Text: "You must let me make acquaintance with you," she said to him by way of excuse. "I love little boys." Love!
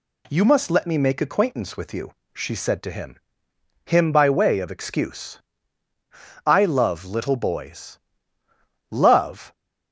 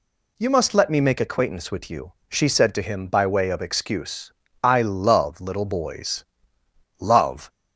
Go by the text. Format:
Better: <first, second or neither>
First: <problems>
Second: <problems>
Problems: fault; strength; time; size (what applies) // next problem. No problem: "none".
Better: second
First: says "him" twice; at 3.8 s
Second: none